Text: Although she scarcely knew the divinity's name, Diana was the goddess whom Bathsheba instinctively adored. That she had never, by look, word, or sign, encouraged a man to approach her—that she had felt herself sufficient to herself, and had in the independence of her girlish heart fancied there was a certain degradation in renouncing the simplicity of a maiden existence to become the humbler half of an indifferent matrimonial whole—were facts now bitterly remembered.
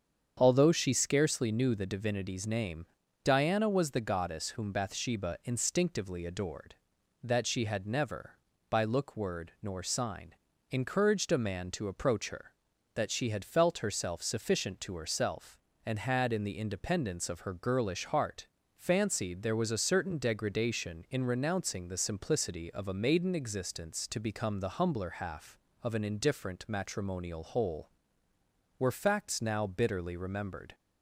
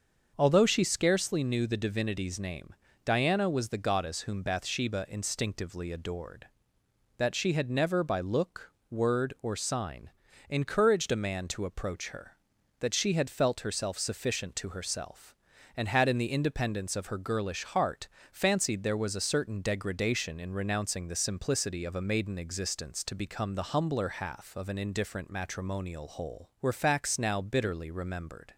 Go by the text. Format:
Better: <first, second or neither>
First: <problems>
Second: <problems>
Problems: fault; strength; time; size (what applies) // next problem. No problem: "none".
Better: second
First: starts louder than the rest; strong; until 1.3 s; 7.5 dB // says "nor" for "or"; at 9.6 s // pauses between "heart" and "fancied"; slight; at 18.4 s; 0.30 s long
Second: starts louder than the rest; until 1.3 s; 6.5 dB // pauses between "heart" and "fancied"; slight; at 18.0 s; 0.24 s long